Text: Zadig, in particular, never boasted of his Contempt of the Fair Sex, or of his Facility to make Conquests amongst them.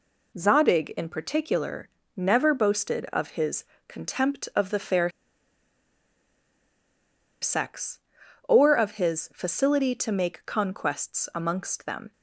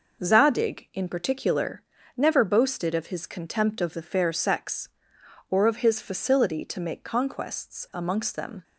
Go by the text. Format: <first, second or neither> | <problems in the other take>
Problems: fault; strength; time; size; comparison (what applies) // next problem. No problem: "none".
second | pauses between "his" and "Contempt"; slight; at 3.6 s; 0.24 s long // pauses between "Fair" and "Sex"; strong; at 5.0 s; 2.3 s long